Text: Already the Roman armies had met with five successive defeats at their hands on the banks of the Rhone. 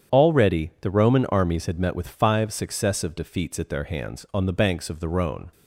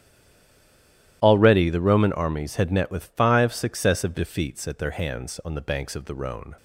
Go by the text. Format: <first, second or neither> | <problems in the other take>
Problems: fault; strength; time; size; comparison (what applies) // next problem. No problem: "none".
first | stays silent before the first word; noticeable; until 1.2 s; 1.2 s long // starts louder than the rest; strong; until 2.2 s; 13 dB; strong in the first